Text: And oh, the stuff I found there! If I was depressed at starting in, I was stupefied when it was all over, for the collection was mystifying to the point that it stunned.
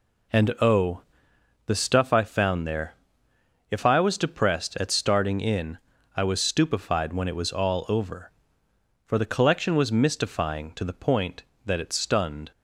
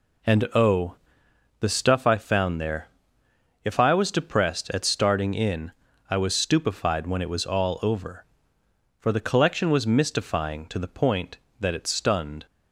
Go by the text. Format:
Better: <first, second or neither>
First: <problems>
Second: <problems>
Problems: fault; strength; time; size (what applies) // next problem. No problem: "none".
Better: neither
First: none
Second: none